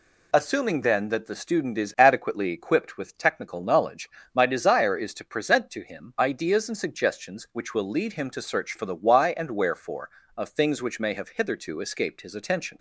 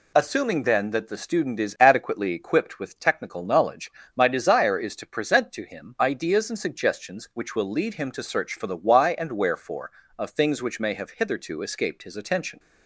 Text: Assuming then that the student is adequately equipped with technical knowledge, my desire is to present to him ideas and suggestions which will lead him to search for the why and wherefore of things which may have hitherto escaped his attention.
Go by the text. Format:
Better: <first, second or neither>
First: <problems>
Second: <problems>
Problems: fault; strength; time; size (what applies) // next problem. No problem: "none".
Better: neither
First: none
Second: none